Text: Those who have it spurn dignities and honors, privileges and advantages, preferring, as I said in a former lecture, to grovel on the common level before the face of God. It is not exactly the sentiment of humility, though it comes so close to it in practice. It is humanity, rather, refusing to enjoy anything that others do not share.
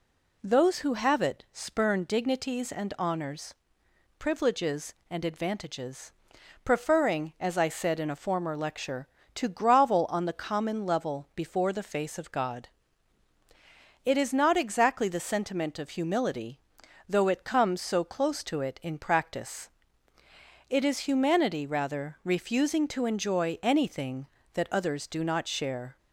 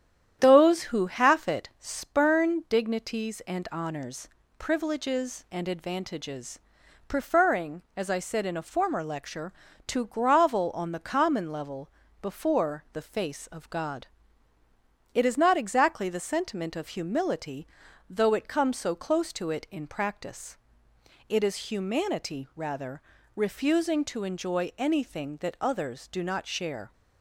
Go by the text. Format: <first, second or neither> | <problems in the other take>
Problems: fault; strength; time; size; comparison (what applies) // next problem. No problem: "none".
first | starts louder than the rest; strong; until 1.4 s; 10 dB // says "half" for "have"; at 1.0 s // pauses between "level" and "before"; slight; at 11.8 s; 0.32 s long